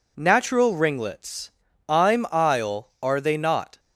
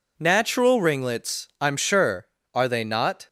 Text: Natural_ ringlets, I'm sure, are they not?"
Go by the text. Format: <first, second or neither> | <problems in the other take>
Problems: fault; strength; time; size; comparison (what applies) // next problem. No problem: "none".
second | says "isle" for "sure"; at 2.3 s